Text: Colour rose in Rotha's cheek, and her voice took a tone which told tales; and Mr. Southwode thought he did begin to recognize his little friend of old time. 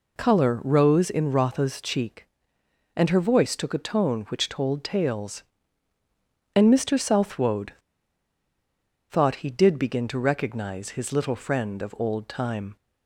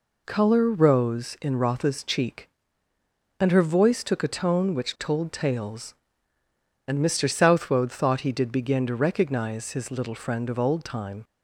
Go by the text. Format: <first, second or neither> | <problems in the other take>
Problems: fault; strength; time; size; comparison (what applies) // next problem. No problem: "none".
second | pauses between "Southwode" and "thought"; strong; at 7.7 s; 1.3 s long